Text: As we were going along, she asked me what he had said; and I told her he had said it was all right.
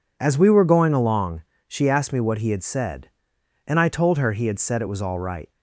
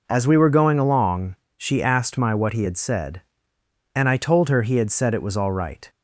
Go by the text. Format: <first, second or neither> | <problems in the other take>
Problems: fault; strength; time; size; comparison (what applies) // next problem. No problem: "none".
first | says "my" for "me"; at 2.1 s